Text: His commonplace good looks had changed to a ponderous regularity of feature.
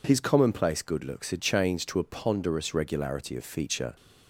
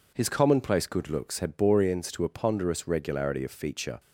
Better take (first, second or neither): first